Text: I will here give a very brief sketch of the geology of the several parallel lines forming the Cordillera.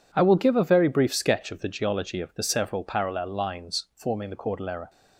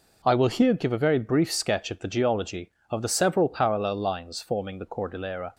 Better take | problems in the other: second | skips "here"; at 0.3 s

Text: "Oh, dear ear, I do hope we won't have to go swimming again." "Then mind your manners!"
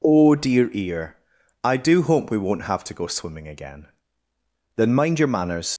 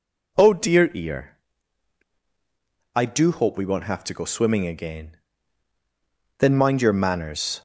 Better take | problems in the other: second | leaves "manners" unfinished; at 5.7 s; 80 ms

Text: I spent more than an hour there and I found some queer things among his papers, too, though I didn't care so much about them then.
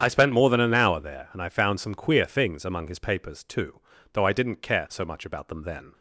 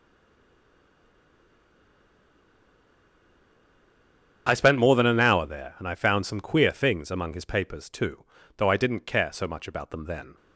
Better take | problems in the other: first | stays silent before the first word; strong; until 4.4 s; 4.4 s long // starts louder than the rest; strong; until 5.4 s; 8.5 dB; strong in the first

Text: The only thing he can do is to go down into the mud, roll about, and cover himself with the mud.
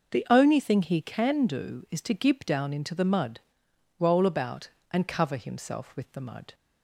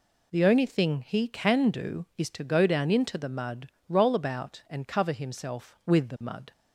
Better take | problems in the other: second | says "gib" for "go"; at 2.1 s

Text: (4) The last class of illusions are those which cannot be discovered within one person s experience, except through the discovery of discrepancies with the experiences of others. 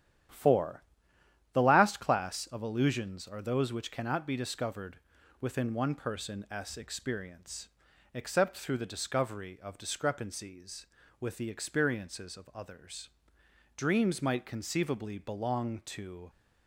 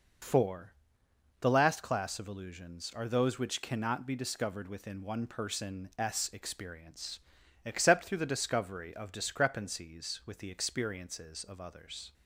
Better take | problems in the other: second | starts louder than the rest; strong; until 1.9 s; 10.5 dB // pauses between "discovered" and "within"; at 4.9 s; 0.42 s long // goes on to say "Dreams might conceivably belong to"; strong; from 13.7 s on; 2.5 s long

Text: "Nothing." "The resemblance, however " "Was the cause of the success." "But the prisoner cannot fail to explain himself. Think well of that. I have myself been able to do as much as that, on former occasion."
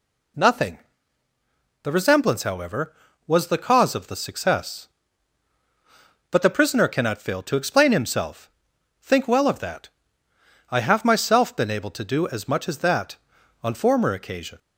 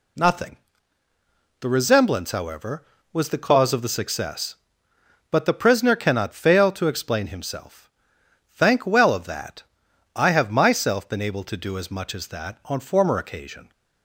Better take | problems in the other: first | says "Thank" for "Think"; at 8.5 s

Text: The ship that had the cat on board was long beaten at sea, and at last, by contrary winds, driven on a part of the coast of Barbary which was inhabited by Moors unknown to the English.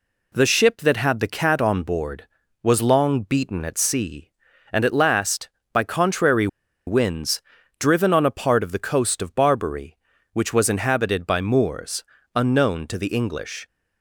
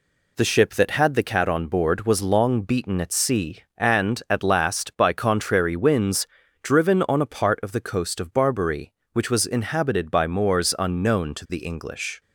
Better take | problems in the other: second | pauses between "contrary" and "winds"; at 6.4 s; 0.39 s long // pauses between "Moors" and "unknown"; slight; at 12.0 s; 0.32 s long

